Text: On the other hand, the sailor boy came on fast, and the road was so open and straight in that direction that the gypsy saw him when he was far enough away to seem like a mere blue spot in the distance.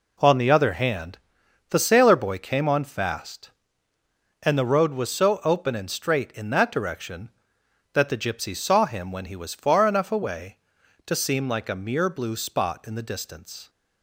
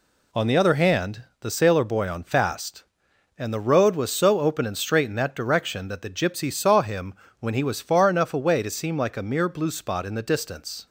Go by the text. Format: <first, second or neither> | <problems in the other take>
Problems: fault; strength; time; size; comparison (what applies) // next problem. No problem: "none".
first | skips "came"; at 2.0 s // pauses between "him" and "when"; slight; at 7.1 s; 0.26 s long